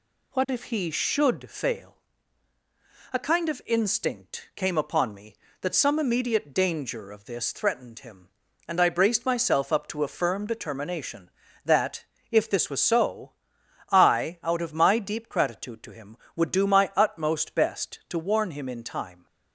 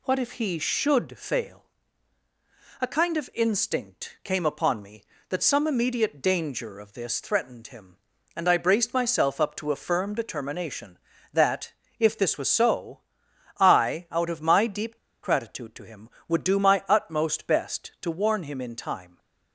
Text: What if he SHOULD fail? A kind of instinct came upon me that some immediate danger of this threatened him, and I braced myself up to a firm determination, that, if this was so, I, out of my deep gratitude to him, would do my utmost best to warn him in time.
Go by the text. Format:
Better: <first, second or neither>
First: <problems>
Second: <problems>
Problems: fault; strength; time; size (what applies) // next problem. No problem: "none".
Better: first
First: none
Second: pauses between "deep" and "gratitude"; slight; at 14.9 s; 0.27 s long